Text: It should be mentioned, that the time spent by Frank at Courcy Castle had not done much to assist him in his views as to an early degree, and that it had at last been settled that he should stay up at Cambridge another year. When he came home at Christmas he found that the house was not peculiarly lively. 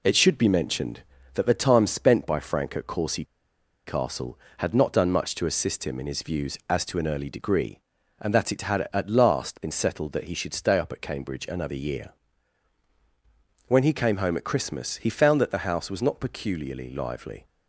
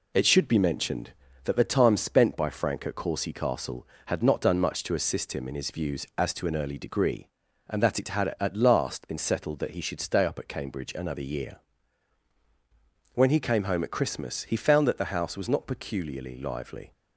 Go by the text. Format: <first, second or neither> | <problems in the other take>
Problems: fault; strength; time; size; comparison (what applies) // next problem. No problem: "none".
second | pauses between "Courcy" and "Castle"; noticeable; at 3.2 s; 0.62 s long